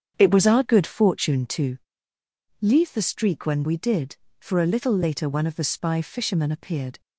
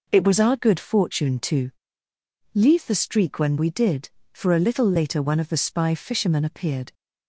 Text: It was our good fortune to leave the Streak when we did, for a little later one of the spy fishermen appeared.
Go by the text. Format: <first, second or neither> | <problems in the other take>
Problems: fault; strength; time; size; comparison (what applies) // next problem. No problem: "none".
second | starts louder than the rest; strong; until 1.5 s; 8 dB // pauses between "to" and "leave"; noticeable; at 1.7 s; 0.84 s long; noticeable in the second